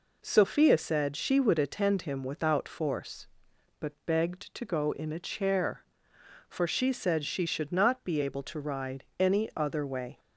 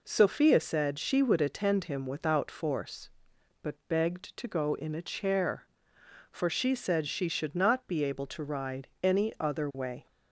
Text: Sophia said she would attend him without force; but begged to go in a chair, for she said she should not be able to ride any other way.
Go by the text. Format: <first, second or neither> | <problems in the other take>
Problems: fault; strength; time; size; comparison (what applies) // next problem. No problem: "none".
neither | pauses between "ride" and "any"; slight; the same in both